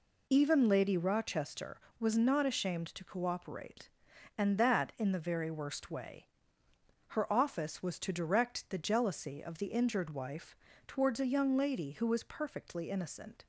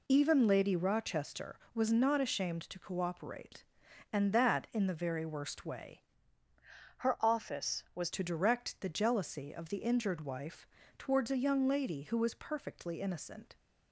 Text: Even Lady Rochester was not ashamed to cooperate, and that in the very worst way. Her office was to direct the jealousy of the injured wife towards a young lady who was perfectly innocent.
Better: first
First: pauses between "wife" and "towards"; slight; at 10.5 s; 0.30 s long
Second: changes voice from "Her" to "was"; from 6.9 to 8.1 s; 1.2 s long // pauses between "wife" and "towards"; slight; at 10.6 s; 0.30 s long

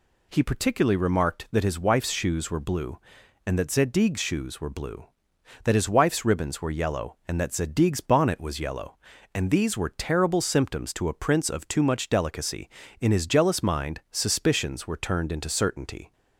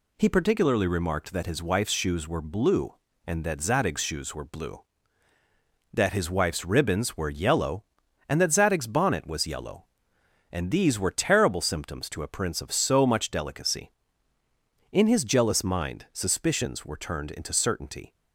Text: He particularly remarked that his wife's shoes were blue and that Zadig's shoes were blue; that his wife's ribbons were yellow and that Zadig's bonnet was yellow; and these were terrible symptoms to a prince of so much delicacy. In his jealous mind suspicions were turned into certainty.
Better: second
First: says "too" for "so"; at 11.6 s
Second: none

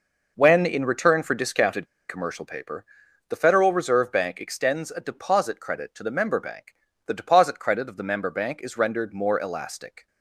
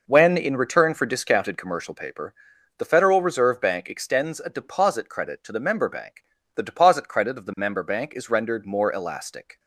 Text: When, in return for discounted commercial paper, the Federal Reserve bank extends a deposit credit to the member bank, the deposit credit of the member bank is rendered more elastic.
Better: second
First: pauses between "discounted" and "commercial"; slight; at 1.8 s; 0.22 s long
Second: none

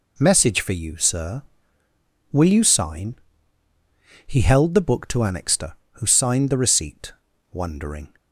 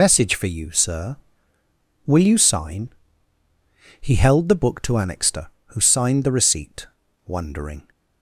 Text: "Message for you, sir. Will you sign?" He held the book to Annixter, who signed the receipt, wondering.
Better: first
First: none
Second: loses the start of "Message"; at 0.0 s; 80 ms

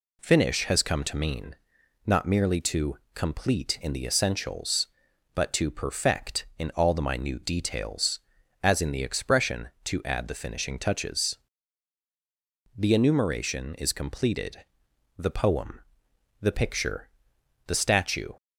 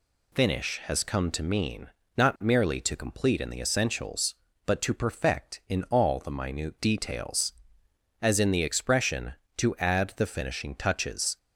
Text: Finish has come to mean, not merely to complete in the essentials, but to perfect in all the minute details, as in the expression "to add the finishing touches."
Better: second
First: pauses between "to" and "complete"; slight; at 2.9 s; 0.16 s long // goes on to say "The enumeration is completed the poem the picture the statue"; strong; from 12.7 s on; 5.5 s long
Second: none

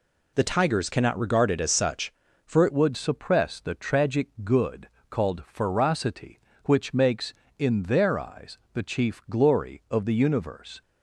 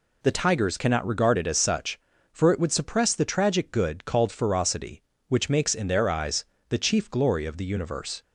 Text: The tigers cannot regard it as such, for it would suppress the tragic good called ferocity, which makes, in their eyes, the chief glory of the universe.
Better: second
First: changes voice at "would"; from 2.7 s on; 8.1 s long // pauses between "tragic" and "good"; slight; at 4.2 s; 0.16 s long // pauses between "good" and "called"; slight; at 4.8 s; 0.22 s long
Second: none

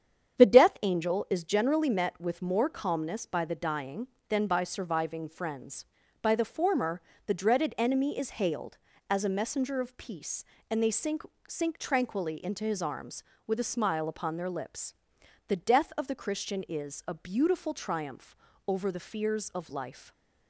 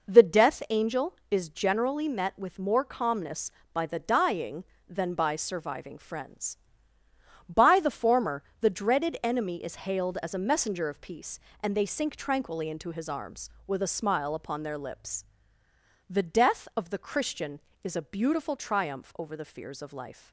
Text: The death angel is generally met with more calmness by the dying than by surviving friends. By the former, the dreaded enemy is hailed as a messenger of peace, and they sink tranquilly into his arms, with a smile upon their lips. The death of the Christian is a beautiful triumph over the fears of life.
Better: second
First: starts louder than the rest; strong; until 1.4 s; 8.5 dB // says "sink" twice; at 11.4 s // pauses between "triumph" and "over"; slight; at 18.3 s; 0.32 s long // stays silent after the last word; slight; from 19.9 s on; 0.5 s long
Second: none

